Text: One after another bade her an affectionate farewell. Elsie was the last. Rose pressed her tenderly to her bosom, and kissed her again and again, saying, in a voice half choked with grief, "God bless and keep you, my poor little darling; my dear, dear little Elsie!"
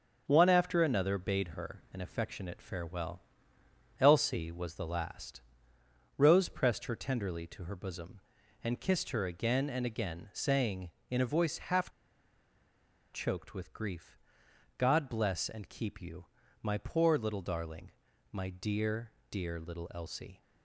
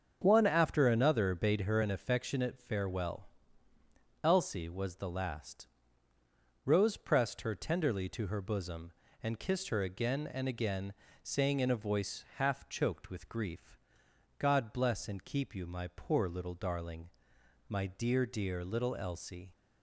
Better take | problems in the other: second | starts louder than the rest; until 1.2 s; 7 dB; also in the second // pauses between "half" and "choked"; at 11.8 s; 1.2 s long

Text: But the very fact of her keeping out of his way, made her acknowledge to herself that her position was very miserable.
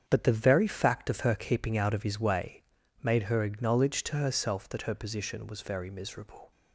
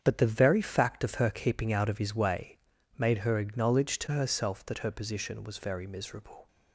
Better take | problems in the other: neither | starts louder than the rest; strong; the same in both

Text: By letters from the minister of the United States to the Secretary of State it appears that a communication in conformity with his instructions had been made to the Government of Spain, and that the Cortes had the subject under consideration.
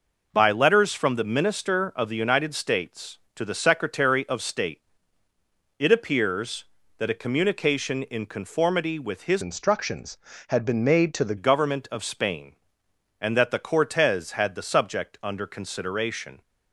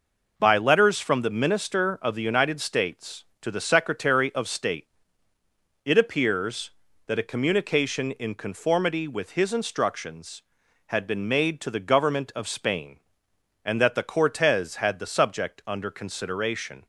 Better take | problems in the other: second | pauses between "State" and "it"; noticeable; at 4.8 s; 0.96 s long; noticeable in the second // changes voice from "instructions" to "the"; from 9.4 to 11.3 s; 1.9 s long

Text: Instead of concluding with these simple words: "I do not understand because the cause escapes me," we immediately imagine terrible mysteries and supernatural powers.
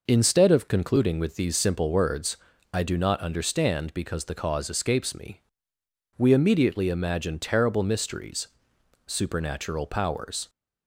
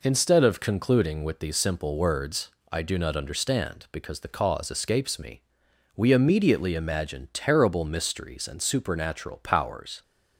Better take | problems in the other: second | skips "and"; at 8.7 s

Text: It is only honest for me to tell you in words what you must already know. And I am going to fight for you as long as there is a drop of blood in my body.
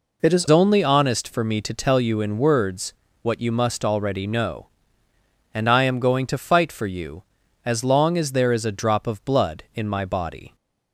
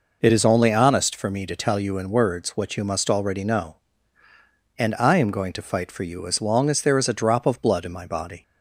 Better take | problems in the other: second | changes voice at "only"; from 0.4 s on; 10.1 s long // pauses between "words" and "what"; slight; at 2.9 s; 0.28 s long

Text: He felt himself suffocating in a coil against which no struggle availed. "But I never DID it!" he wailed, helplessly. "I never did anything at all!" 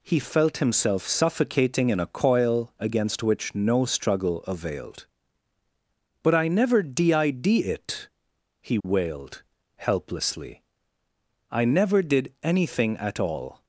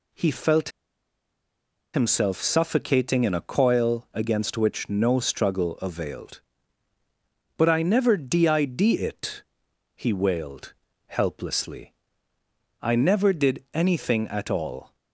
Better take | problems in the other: first | pauses between "felt" and "himself"; at 0.7 s; 1.2 s long

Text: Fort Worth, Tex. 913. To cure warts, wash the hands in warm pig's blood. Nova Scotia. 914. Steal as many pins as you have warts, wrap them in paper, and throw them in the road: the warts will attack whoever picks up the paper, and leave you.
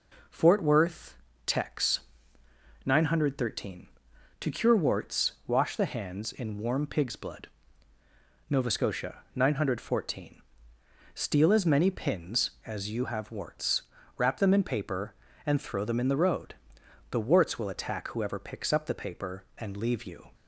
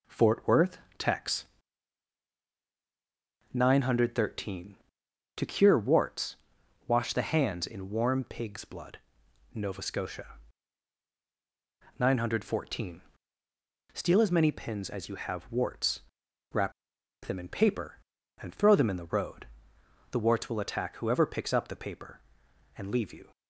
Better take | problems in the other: first | pauses between "wrap" and "them"; noticeable; at 16.7 s; 0.52 s long

